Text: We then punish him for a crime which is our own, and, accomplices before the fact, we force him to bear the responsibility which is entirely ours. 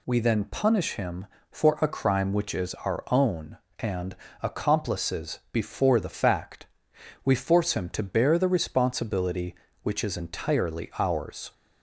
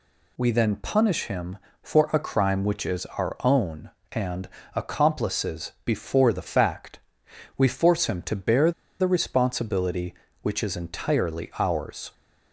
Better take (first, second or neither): first